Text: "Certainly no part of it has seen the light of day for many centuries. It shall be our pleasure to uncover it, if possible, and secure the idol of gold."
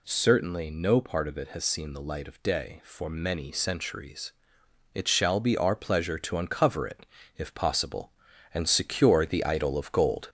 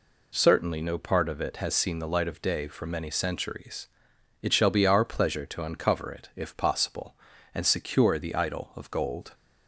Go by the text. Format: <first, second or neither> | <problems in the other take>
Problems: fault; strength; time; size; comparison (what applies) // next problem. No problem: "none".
second | gets louder; slight; throughout; 3 dB